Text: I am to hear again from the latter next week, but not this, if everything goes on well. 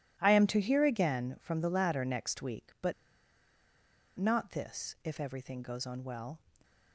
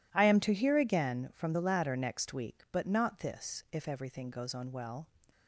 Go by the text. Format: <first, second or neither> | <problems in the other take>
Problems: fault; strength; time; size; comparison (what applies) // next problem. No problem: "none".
second | pauses between "but" and "not"; strong; at 2.9 s; 1.2 s long